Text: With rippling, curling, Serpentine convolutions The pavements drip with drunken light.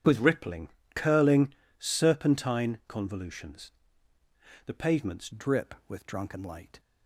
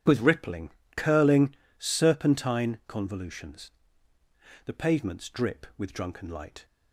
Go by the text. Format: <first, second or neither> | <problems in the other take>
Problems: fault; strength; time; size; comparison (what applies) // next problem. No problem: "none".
second | starts louder than the rest; strong; until 1.3 s; 9 dB // pauses between "convolutions" and "The"; noticeable; at 3.7 s; 0.94 s long; noticeable in the second // changes voice at "drip"; from 5.3 s on; 1.4 s long